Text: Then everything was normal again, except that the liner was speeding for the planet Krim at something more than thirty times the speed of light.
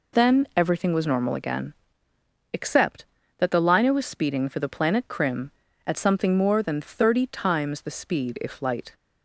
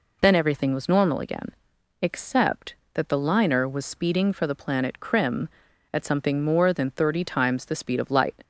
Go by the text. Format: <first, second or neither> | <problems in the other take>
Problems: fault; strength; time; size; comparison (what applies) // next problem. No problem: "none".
second | says "if" for "of"; at 8.4 s